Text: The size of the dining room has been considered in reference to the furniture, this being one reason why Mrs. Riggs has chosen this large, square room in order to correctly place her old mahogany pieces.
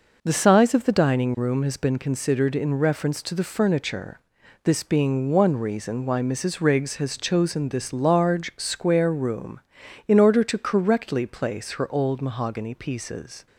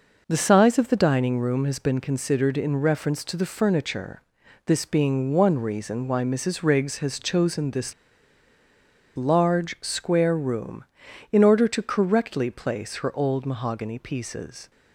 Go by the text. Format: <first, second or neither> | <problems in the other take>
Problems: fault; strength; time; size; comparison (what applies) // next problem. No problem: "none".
first | pauses between "this" and "large"; at 7.9 s; 1.2 s long